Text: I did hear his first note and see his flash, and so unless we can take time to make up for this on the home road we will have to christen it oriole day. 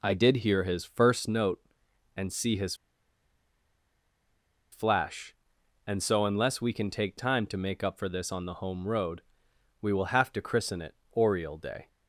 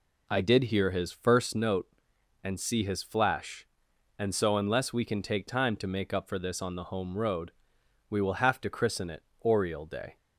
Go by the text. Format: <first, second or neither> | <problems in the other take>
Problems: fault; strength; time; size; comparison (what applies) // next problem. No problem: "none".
second | pauses between "his" and "flash"; strong; at 2.7 s; 1.9 s long // pauses between "road" and "we"; noticeable; at 9.2 s; 0.60 s long; noticeable in the second // pauses between "it" and "oriole"; slight; at 10.9 s; 0.18 s long; slight in the second